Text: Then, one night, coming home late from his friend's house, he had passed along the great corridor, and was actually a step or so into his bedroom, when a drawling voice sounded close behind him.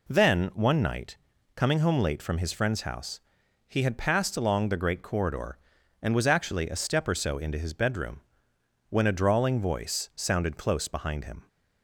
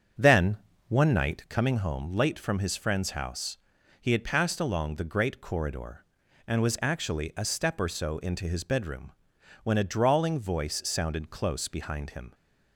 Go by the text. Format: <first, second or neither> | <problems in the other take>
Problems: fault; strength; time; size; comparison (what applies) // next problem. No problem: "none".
first | starts louder than the rest; strong; until 1.7 s; 7.5 dB